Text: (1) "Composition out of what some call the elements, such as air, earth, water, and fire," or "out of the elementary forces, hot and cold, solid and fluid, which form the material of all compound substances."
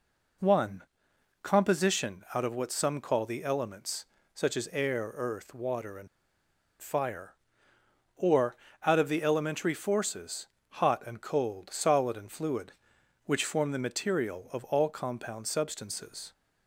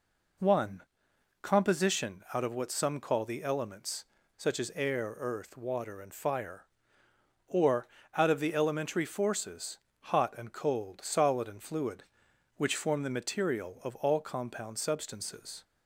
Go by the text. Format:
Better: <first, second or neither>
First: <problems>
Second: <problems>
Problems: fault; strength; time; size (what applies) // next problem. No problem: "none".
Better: second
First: pauses between "and" and "fire"; noticeable; at 6.0 s; 0.71 s long // pauses between "or" and "out"; slight; at 8.5 s; 0.30 s long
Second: pauses between "or" and "out"; slight; at 7.8 s; 0.30 s long